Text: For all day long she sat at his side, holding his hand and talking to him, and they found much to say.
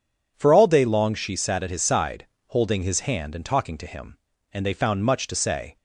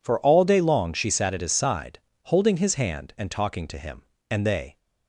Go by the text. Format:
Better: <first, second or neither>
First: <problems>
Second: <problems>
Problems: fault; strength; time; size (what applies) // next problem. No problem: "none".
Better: first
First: none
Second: stops before "found much to say"; at 4.7 s